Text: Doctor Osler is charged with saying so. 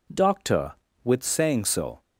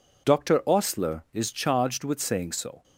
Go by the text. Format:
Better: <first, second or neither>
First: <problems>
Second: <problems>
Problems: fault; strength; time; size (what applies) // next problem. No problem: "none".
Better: second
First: skips "Osler is charged"; at 0.8 s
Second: none